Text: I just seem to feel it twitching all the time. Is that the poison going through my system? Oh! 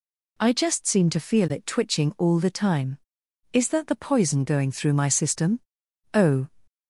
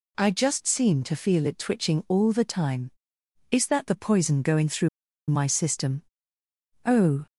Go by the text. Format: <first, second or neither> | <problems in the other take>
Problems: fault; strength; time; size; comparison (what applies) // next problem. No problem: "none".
first | pauses between "through" and "my"; at 4.8 s; 0.41 s long